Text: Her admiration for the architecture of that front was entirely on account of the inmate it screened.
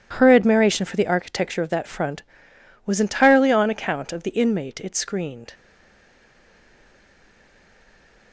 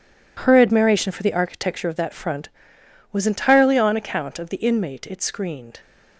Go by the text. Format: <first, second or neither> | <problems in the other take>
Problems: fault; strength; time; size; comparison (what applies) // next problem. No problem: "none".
second | stays silent after the last word; strong; from 5.5 s on; 2.8 s long